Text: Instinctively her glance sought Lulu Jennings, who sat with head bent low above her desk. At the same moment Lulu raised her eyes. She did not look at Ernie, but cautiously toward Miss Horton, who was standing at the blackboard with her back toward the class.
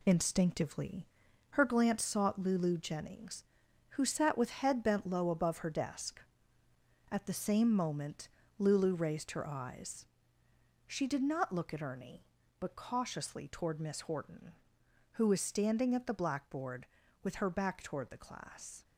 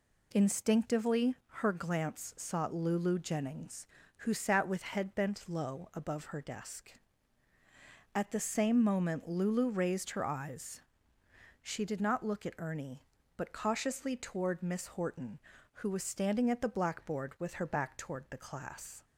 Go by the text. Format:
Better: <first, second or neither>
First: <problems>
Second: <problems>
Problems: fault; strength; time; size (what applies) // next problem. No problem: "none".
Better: second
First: gets quieter; throughout; 6.5 dB // pauses between "Instinctively" and "her"; at 1.0 s; 0.44 s long // pauses between "moment" and "Lulu"; slight; at 8.2 s; 0.30 s long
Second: none